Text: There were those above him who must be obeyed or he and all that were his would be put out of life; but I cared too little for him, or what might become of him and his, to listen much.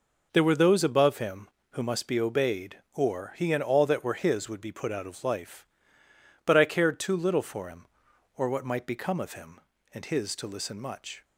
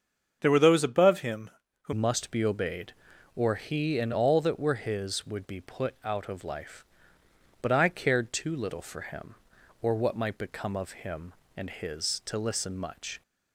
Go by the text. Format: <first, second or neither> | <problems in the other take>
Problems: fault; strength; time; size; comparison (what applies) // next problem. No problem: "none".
first | starts louder than the rest; until 1.4 s; 7 dB // changes voice at "must"; from 1.9 s on; 11.3 s long